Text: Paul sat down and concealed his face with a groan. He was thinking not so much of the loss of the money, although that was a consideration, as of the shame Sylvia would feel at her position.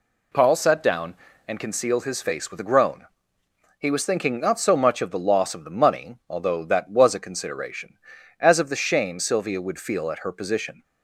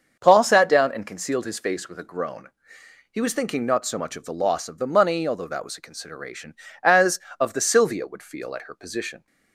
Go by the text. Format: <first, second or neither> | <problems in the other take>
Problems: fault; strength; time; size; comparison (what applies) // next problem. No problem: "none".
first | starts louder than the rest; until 1.2 s; 7 dB // skips "shame"; at 7.6 s